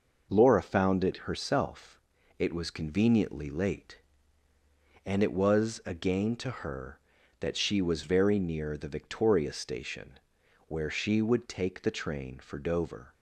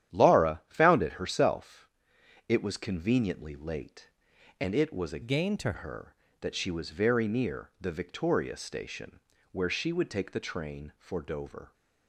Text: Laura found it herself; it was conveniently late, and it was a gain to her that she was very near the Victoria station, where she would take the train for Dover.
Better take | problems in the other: first | starts louder than the rest; strong; until 1.2 s; 11 dB // changes voice from "gain" to "to"; from 5.2 to 5.7 s; 0.5 s long

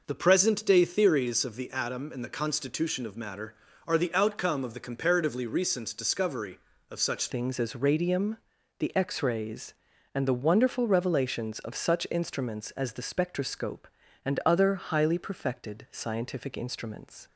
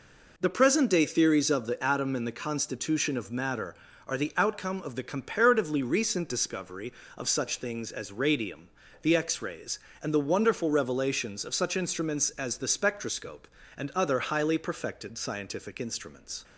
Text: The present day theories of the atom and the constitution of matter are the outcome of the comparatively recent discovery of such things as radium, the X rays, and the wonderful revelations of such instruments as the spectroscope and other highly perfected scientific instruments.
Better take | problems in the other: second | changes voice at "things"; from 7.2 s on; 10.0 s long

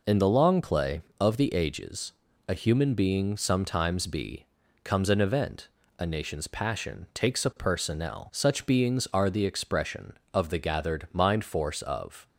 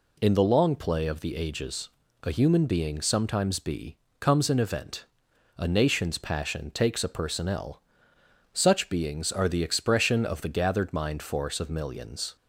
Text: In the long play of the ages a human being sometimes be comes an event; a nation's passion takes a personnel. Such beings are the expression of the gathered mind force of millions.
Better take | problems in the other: second | pauses between "ages" and "a"; at 2.1 s; 0.38 s long; slight in the second // pauses between "be" and "comes"; slight; at 4.4 s; 0.36 s long; slight in the second // stops before "millions"; at 12.2 s

